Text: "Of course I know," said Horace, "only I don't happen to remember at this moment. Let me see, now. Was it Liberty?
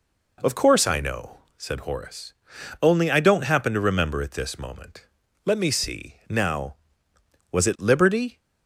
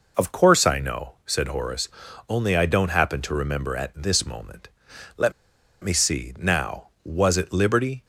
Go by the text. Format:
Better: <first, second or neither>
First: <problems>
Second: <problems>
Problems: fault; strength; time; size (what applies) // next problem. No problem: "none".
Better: first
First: none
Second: pauses between "Let" and "me"; noticeable; at 5.3 s; 0.52 s long